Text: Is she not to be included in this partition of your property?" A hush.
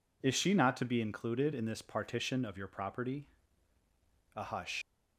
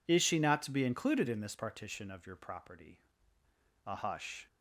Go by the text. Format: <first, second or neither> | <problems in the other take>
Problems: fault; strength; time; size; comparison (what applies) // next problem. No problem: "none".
second | leaves "hush" unfinished; at 4.8 s; 100 ms